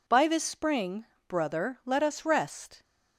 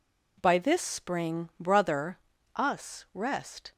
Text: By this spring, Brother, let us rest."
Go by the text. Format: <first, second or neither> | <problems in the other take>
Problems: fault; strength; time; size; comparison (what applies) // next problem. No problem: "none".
first | skips "let"; at 2.3 s